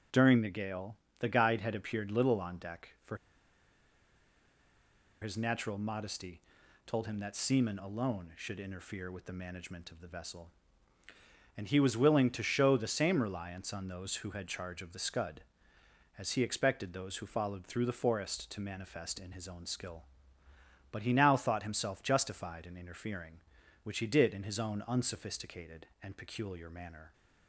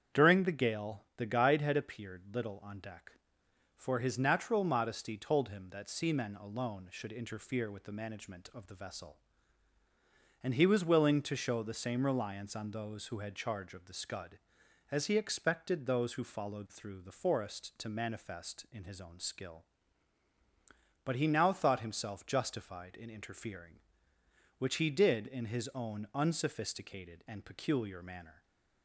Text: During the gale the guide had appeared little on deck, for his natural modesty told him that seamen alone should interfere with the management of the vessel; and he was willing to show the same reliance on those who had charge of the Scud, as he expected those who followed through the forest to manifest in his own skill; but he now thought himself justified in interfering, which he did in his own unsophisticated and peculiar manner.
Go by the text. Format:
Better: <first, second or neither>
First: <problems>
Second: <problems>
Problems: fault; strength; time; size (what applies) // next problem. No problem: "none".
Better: second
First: starts louder than the rest; strong; until 1.3 s; 7 dB // pauses between "gale" and "the"; slight; at 0.9 s; 0.22 s long // pauses between "for" and "his"; strong; at 3.1 s; 2.0 s long // pauses between "modesty" and "told"; noticeable; at 6.4 s; 0.46 s long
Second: starts louder than the rest; strong; until 1.2 s; 8 dB